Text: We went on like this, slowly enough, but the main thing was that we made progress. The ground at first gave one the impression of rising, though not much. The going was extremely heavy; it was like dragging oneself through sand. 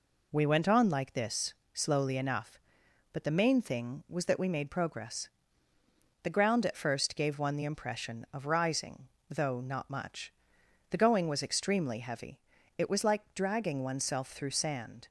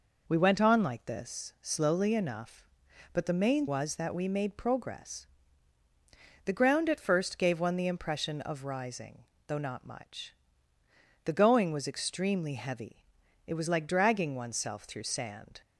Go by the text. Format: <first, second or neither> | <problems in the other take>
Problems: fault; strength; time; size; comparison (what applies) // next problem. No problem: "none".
first | skips "thing"; at 3.6 s